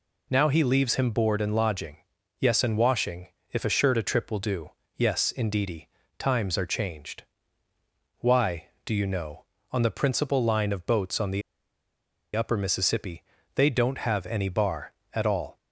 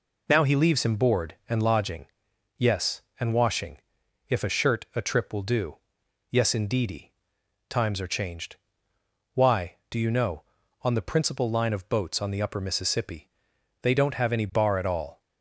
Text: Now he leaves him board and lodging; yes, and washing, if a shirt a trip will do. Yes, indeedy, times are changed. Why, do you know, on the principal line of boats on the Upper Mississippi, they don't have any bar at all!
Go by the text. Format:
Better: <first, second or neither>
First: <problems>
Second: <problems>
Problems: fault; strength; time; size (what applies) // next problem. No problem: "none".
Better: second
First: pauses between "the" and "Upper"; noticeable; at 11.4 s; 0.93 s long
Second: none